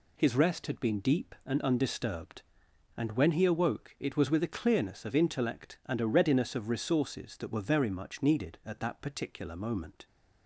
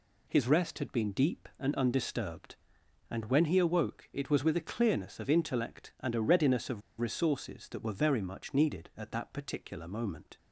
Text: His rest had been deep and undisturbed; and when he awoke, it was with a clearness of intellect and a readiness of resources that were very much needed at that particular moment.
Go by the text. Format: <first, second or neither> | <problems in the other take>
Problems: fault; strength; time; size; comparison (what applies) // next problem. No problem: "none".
first | pauses between "of" and "resources"; slight; at 6.8 s; 0.19 s long